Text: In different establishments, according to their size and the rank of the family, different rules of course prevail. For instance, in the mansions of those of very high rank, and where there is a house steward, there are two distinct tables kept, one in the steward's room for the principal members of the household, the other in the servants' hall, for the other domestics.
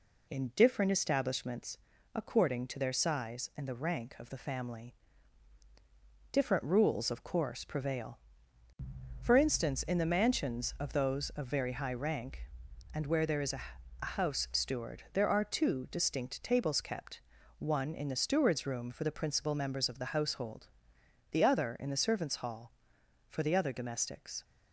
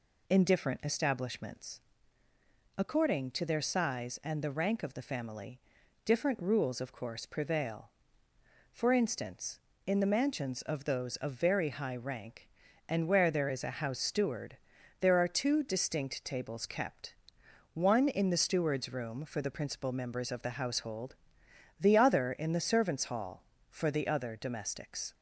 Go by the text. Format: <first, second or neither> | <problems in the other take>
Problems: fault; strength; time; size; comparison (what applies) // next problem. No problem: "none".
second | says "a" twice; at 13.9 s